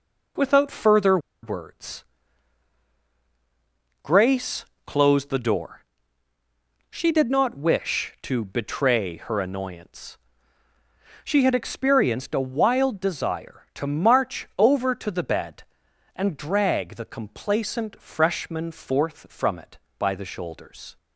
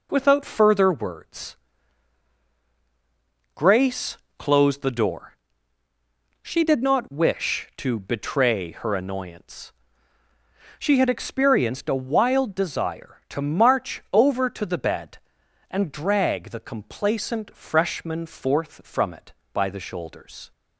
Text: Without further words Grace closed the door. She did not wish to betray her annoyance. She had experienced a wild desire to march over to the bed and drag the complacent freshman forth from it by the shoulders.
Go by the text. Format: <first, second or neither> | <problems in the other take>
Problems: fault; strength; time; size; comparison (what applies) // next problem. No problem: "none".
second | pauses between "further" and "words"; slight; at 1.1 s; 0.24 s long // pauses between "words" and "Grace"; strong; at 2.0 s; 1.9 s long; strong in the second // pauses between "Grace" and "closed"; slight; at 4.6 s; 0.22 s long; slight in the second